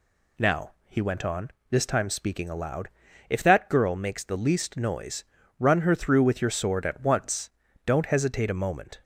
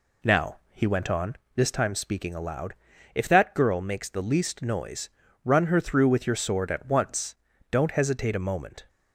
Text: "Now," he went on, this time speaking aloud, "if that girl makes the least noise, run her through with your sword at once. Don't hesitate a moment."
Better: first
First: none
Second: starts louder than the rest; slight; until 1.7 s; 2 dB

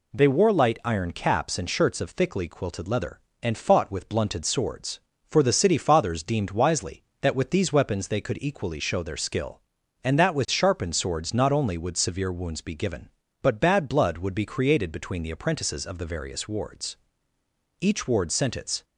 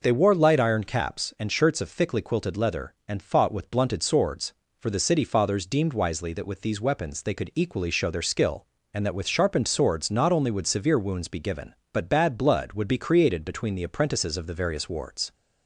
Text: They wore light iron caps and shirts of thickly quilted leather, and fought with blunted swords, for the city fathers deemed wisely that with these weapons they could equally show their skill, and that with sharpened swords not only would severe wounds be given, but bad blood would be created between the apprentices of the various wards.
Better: second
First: goes on to say "Each ward sent its"; noticeable; from 17.7 s on; 1.0 s long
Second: none

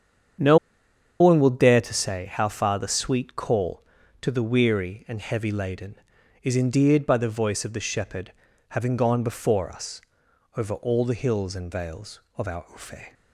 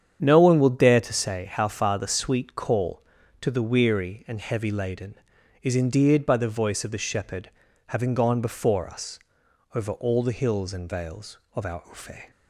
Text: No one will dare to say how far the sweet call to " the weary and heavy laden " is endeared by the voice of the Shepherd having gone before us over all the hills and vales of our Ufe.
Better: second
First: starts louder than the rest; strong; until 2.0 s; 8.5 dB // pauses between "No" and "one"; noticeable; at 0.5 s; 0.62 s long // pauses between "Shepherd" and "having"; at 8.3 s; 0.38 s long // pauses between "us" and "over"; noticeable; at 9.9 s; 0.56 s long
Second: starts louder than the rest; strong; until 1.2 s; 8.5 dB // pauses between "Shepherd" and "having"; at 7.4 s; 0.38 s long // pauses between "us" and "over"; noticeable; at 9.1 s; 0.56 s long

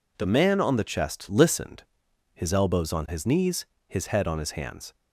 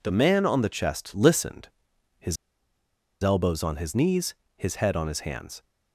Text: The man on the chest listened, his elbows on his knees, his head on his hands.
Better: first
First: none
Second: pauses between "his" and "elbows"; noticeable; at 2.3 s; 0.87 s long

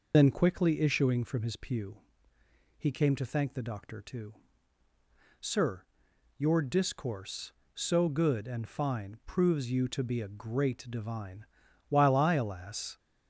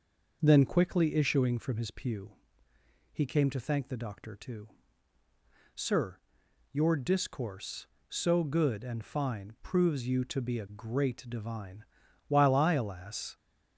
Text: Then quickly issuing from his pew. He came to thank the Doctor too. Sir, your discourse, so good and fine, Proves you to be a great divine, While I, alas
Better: second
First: loses the start of "Then"; at 0.1 s; 75 ms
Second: none

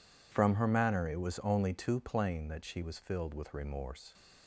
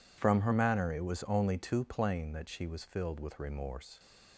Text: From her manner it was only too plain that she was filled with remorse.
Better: neither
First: none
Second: none

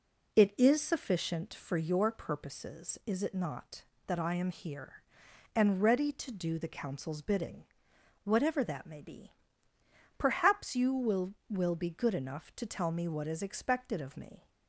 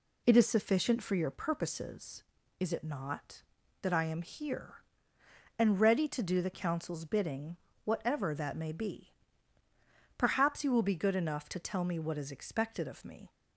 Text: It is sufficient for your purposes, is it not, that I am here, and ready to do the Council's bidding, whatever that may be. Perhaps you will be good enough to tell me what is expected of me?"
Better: second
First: says "will" twice; at 11.4 s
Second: none

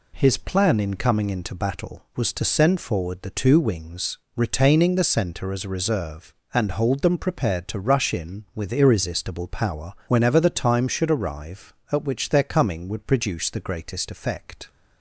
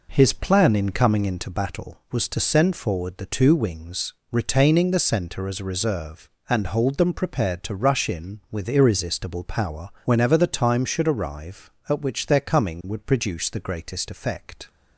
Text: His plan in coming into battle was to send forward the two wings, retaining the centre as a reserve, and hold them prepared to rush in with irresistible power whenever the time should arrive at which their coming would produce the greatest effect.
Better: first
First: pauses between "power" and "whenever"; slight; at 9.9 s; 0.15 s long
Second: starts louder than the rest; noticeable; until 1.6 s; 4.5 dB // pauses between "power" and "whenever"; slight; at 9.9 s; 0.16 s long

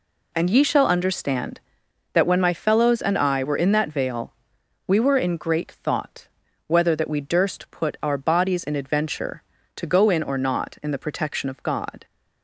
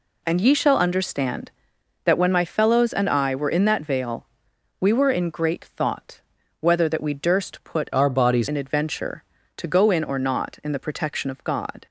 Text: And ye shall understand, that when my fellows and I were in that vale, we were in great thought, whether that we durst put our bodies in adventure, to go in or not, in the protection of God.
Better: first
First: none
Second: changes voice from "our" to "bodies"; from 7.9 to 8.4 s; 0.5 s long

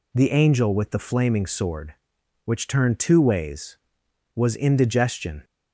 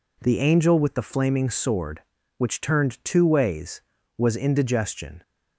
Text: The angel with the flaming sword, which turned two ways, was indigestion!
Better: neither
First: none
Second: none

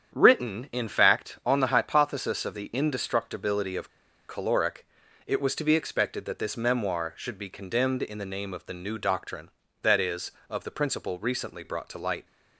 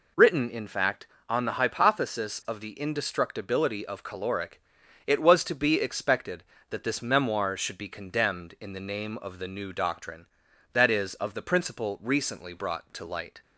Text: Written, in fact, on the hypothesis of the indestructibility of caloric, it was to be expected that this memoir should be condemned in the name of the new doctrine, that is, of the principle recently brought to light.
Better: second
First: starts louder than the rest; strong; until 1.1 s; 8.5 dB // pauses between "of" and "caloric"; at 3.8 s; 0.39 s long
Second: none

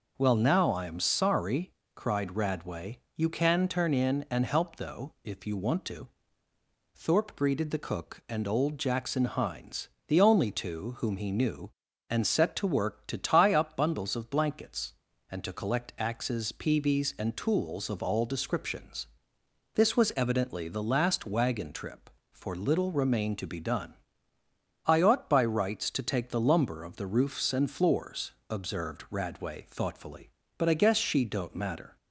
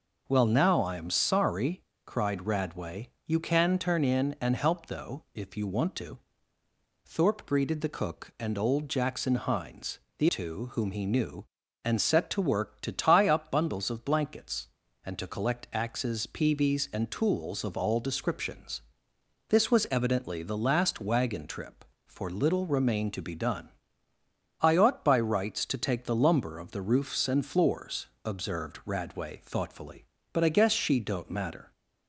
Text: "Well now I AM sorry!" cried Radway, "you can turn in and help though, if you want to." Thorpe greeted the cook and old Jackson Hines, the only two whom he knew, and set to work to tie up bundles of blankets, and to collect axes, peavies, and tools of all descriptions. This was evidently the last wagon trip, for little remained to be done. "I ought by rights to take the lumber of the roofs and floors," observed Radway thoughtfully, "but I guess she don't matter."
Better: first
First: none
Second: skips "only"; at 10.2 s

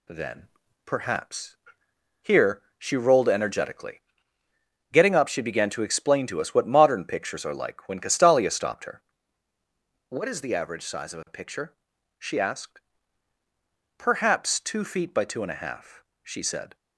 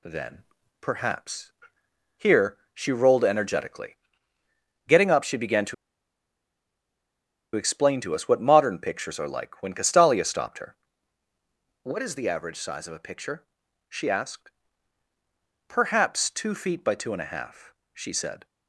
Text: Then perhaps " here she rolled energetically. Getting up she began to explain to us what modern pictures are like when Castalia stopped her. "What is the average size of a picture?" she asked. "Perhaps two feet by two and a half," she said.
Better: first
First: pauses between "Then" and "perhaps"; at 0.4 s; 0.38 s long // pauses between "here" and "she"; slight; at 2.6 s; 0.16 s long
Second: pauses between "Then" and "perhaps"; at 0.4 s; 0.38 s long // pauses between "here" and "she"; slight; at 2.5 s; 0.16 s long // pauses between "to" and "explain"; strong; at 5.7 s; 1.8 s long

